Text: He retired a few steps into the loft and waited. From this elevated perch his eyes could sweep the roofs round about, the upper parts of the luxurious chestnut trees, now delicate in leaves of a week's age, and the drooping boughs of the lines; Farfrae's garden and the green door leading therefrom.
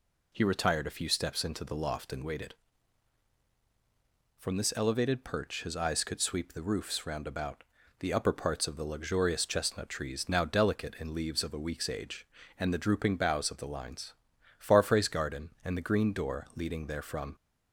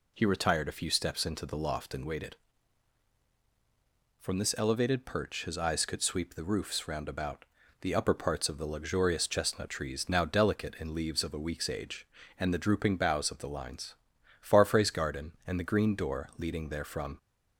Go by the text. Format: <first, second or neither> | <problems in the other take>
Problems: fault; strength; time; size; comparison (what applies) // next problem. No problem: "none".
neither | none